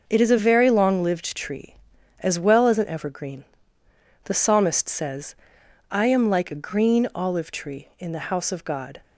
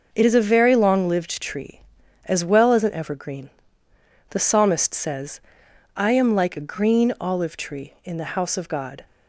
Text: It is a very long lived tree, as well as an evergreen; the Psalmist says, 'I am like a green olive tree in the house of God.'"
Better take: neither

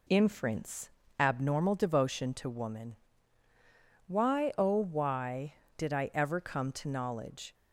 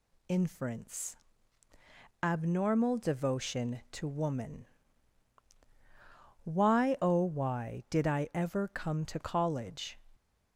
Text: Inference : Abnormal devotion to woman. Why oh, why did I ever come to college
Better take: second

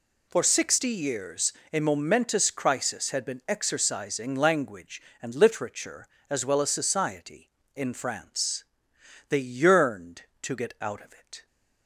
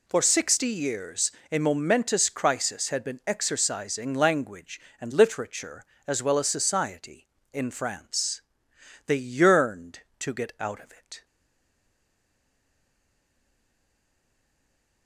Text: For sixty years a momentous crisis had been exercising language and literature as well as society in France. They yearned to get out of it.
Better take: first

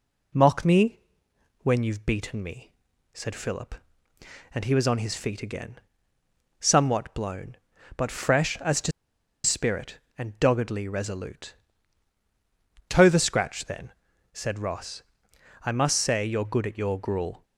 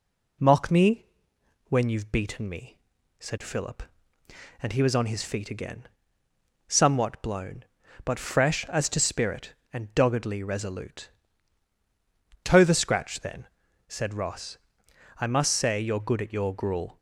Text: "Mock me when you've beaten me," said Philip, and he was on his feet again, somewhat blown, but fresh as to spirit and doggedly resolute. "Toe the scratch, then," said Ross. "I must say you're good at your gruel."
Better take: second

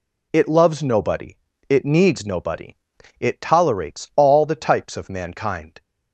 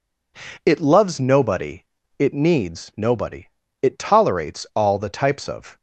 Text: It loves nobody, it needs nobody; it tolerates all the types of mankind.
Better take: first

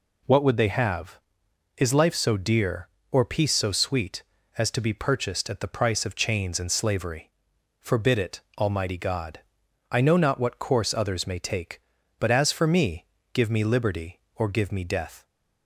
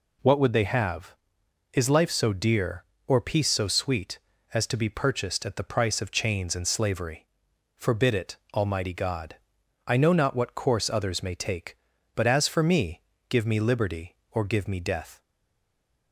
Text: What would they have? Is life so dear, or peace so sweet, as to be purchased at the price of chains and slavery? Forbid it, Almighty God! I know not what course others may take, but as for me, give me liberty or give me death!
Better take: first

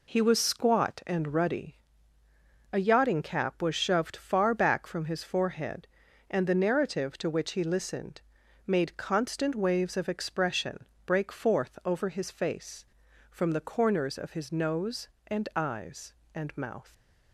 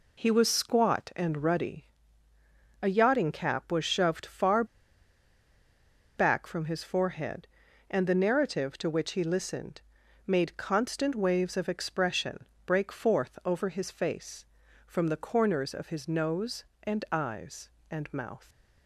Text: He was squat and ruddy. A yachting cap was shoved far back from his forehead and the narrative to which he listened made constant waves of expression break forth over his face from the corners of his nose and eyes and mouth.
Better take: first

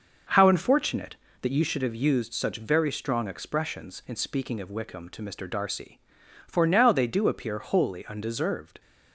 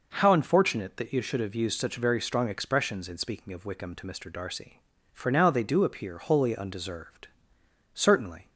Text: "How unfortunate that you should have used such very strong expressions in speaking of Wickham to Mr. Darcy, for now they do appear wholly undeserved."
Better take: first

